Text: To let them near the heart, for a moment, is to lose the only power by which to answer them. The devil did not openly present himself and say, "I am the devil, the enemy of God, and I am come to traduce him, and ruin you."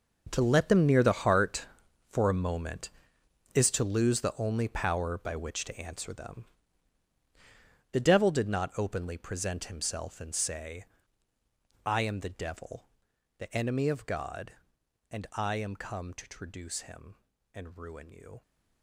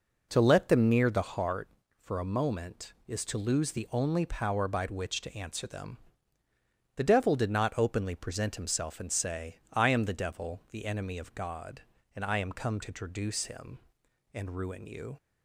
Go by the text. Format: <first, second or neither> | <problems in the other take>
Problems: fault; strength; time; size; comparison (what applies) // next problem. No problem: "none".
second | gets quieter; strong; throughout; 15 dB